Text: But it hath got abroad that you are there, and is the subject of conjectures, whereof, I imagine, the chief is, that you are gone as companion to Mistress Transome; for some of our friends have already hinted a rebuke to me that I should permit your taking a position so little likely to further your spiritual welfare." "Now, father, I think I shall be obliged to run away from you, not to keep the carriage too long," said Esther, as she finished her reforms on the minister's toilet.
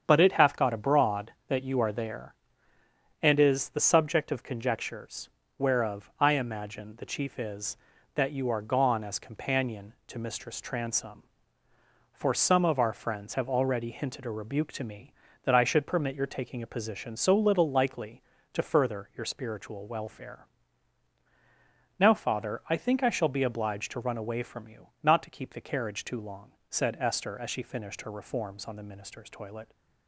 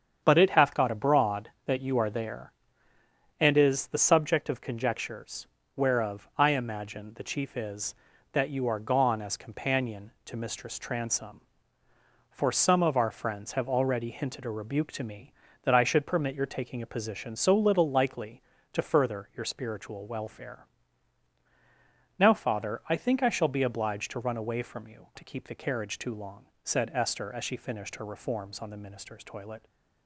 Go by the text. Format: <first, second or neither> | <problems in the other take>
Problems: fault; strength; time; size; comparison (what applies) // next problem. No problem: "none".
first | starts louder than the rest; strong; until 1.2 s; 7.5 dB; strong in the first // skips "not"; at 25.1 s